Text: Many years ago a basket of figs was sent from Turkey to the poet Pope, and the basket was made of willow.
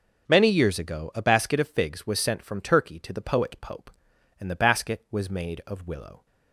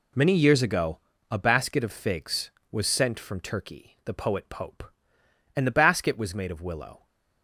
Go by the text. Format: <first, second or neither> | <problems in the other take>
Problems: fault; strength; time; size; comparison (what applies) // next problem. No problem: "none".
first | pauses between "ago" and "a"; slight; at 0.9 s; 0.30 s long // skips "to"; at 4.0 s